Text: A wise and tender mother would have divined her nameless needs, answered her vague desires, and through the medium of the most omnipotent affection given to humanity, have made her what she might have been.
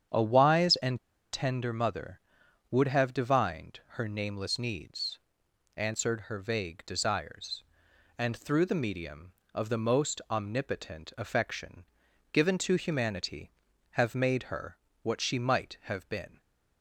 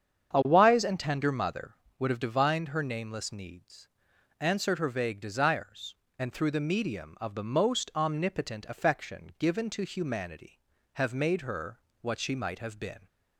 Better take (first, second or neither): second